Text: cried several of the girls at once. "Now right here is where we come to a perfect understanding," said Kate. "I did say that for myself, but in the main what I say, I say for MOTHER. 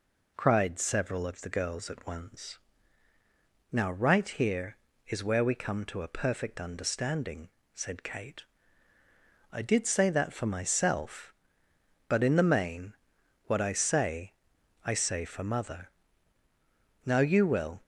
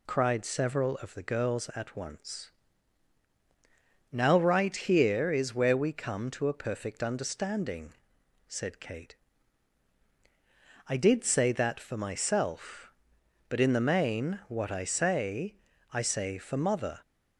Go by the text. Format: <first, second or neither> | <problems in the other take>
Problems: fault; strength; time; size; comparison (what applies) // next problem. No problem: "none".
second | pauses between "main" and "what"; noticeable; at 12.9 s; 0.52 s long // goes on to say "Now you will"; noticeable; from 17.0 s on; 0.78 s long